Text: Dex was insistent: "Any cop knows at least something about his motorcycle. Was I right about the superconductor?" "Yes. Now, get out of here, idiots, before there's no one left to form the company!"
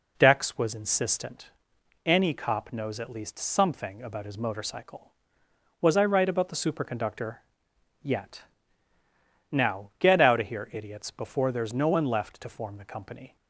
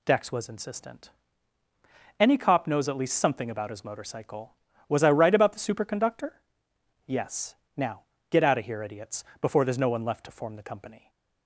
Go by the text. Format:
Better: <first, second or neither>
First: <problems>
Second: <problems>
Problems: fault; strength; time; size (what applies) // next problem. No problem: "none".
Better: second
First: says "Yet" for "Yes"; at 8.0 s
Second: none